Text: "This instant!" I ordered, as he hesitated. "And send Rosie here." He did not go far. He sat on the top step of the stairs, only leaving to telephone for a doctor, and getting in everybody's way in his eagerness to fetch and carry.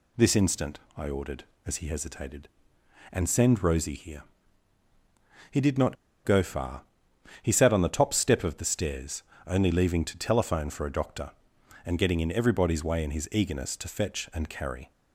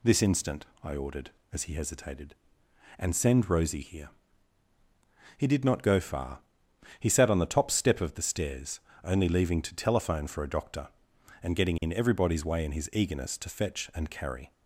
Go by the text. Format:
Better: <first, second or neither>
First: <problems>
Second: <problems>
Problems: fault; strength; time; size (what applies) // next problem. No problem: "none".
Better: second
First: pauses between "not" and "go"; slight; at 5.9 s; 0.29 s long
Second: none